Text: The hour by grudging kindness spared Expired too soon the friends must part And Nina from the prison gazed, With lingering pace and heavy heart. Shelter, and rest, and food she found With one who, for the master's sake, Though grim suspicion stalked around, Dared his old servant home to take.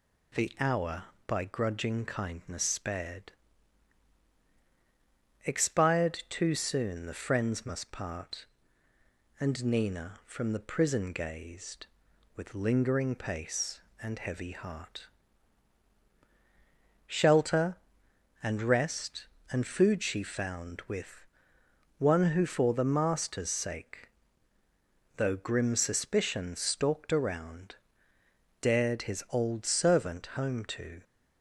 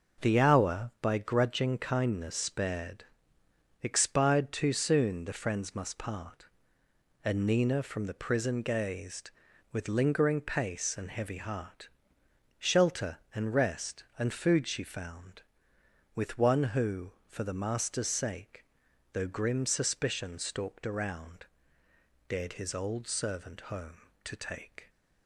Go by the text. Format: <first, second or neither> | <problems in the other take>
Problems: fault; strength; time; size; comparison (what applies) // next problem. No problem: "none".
second | pauses between "spared" and "Expired"; strong; at 3.3 s; 2.1 s long; noticeable in the second // pauses between "With" and "one"; noticeable; at 21.2 s; 0.72 s long // stops before "take"; at 31.0 s